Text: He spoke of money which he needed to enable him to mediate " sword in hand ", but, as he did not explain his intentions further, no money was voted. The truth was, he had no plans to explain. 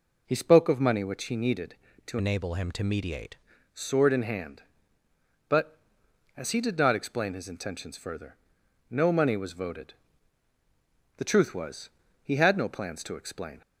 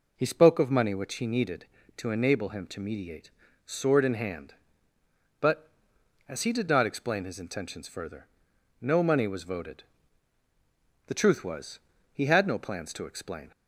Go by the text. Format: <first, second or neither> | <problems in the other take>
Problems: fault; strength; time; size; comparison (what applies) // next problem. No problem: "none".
second | changes voice from "enable" to "mediate"; from 2.1 to 3.3 s; 1.2 s long